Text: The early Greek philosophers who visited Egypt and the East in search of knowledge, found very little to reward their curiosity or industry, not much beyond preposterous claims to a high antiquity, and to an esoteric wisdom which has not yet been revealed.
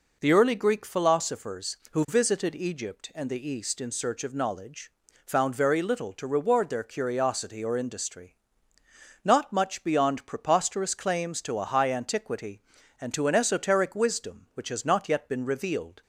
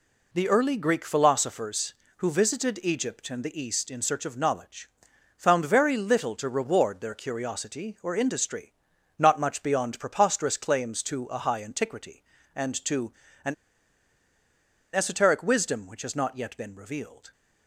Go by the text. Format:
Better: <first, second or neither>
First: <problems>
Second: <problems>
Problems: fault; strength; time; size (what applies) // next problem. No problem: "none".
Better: first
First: none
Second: pauses between "to" and "an"; slight; at 13.1 s; 0.32 s long // pauses between "an" and "esoteric"; strong; at 13.5 s; 1.4 s long